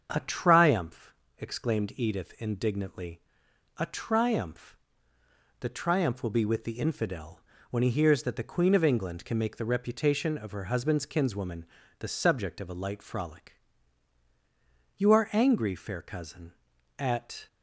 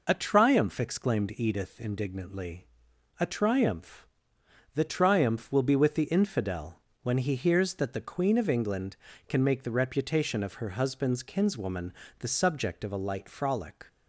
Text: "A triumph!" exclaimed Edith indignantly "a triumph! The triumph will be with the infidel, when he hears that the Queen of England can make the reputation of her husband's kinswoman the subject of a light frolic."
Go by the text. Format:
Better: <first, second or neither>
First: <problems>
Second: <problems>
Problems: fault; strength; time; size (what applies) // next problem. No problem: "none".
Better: second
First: starts louder than the rest; until 1.1 s; 7 dB // pauses between "indignantly" and "a"; noticeable; at 3.2 s; 0.58 s long // pauses between "kinswoman" and "the"; slight; at 11.6 s; 0.34 s long // goes on to say "You are angry fair cousin at"; strong; from 14.9 s on; 2.5 s long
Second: pauses between "indignantly" and "a"; noticeable; at 2.6 s; 0.52 s long // pauses between "kinswoman" and "the"; slight; at 11.9 s; 0.28 s long